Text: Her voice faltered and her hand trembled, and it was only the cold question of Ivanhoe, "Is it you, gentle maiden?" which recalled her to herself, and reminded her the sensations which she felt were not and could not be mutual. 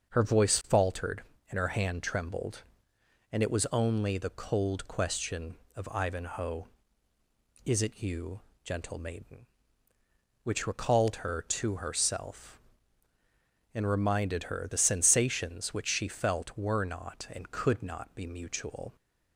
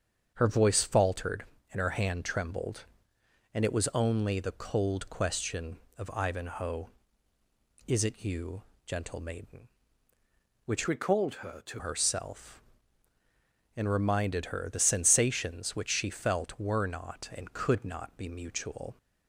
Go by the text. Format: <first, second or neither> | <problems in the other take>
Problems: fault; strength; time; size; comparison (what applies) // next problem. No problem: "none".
first | starts louder than the rest; strong; until 1.3 s; 7.5 dB; also in the first // changes voice from "recalled" to "to"; from 10.8 to 11.8 s; 1.0 s long